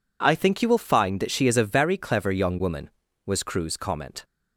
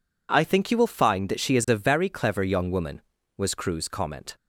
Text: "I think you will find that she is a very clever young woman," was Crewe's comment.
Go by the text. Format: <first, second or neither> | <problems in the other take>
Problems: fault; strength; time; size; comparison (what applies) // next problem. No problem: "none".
neither | none